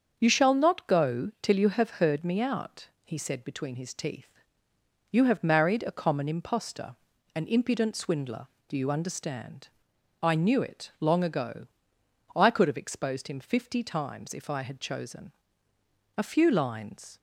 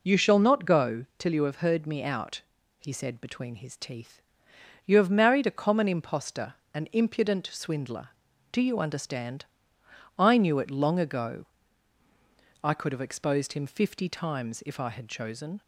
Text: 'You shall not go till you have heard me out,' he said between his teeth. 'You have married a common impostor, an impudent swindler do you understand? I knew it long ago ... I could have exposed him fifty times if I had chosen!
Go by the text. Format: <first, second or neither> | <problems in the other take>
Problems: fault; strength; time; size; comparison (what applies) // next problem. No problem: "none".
second | starts louder than the rest; until 1.1 s; 7 dB // goes on to say "A few lines"; noticeable; from 16.1 s on; 1.0 s long